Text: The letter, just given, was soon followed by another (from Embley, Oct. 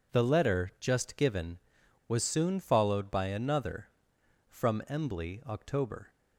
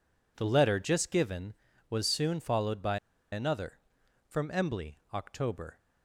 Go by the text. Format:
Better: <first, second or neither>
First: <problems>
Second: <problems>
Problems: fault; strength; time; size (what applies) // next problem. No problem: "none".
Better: first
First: none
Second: pauses between "by" and "another"; slight; at 2.9 s; 0.35 s long